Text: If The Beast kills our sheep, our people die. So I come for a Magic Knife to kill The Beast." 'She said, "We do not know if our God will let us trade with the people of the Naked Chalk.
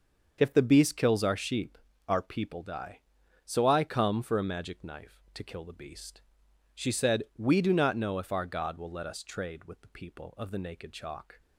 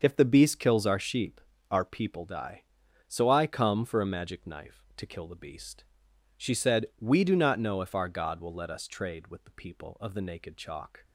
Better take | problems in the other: neither | starts louder than the rest; the same in both

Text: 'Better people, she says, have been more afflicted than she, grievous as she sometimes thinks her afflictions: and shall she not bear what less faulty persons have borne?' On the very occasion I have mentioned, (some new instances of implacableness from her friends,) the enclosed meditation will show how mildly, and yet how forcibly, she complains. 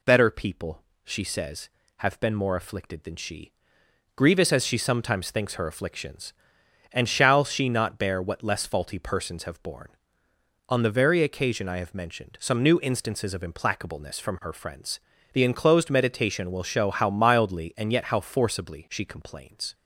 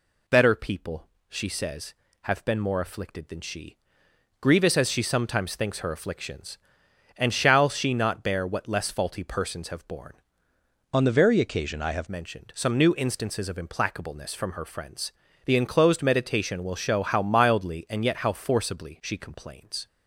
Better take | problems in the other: first | changes voice from "On" to "have"; from 10.9 to 12.0 s; 1.1 s long

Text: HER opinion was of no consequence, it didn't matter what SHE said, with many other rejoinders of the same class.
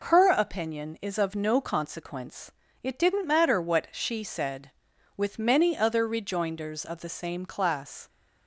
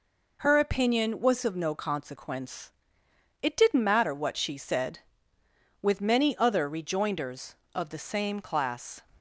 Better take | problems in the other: second | says "is" for "was"; at 1.0 s

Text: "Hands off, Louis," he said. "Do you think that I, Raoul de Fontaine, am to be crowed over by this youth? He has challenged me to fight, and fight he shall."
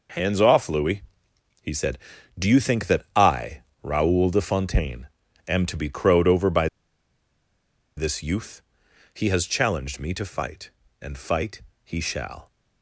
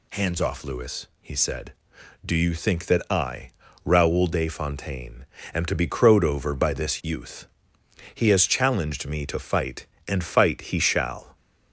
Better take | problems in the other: second | pauses between "by" and "this"; strong; at 6.6 s; 1.3 s long // pauses between "fight" and "he"; slight; at 11.6 s; 0.22 s long

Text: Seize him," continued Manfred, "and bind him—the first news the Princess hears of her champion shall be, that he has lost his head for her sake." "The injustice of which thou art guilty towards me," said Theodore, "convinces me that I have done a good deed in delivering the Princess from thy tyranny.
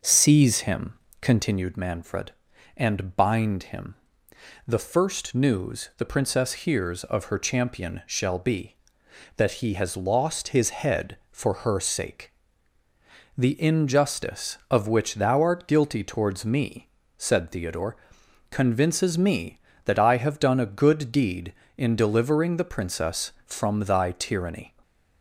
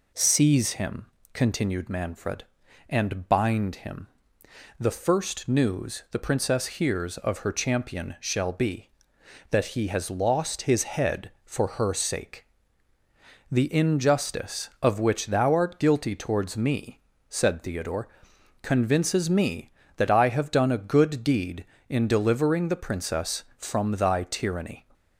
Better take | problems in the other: second | starts louder than the rest; until 1.6 s; 6 dB // stays silent after the last word; slight; from 24.6 s on; 0.6 s long

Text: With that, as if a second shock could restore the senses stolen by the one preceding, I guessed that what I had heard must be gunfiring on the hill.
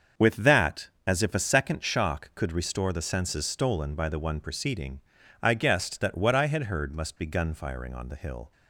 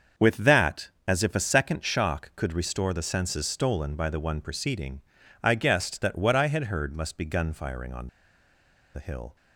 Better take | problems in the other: first | starts louder than the rest; until 1.3 s; 6.5 dB; also in the first // pauses between "on" and "the"; noticeable; at 8.0 s; 0.86 s long

